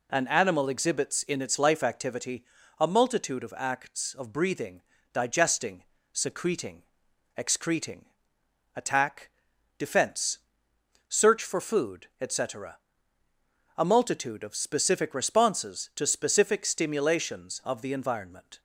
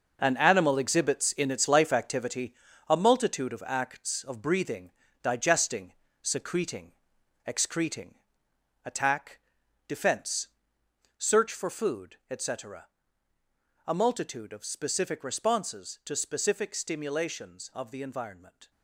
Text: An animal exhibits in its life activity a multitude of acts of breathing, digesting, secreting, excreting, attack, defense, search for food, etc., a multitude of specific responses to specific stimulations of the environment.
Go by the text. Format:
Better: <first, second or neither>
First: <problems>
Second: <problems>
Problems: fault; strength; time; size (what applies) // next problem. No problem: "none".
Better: first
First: pauses between "activity" and "a"; slight; at 2.4 s; 0.36 s long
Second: gets quieter; strong; throughout; 10.5 dB // pauses between "activity" and "a"; slight; at 2.5 s; 0.36 s long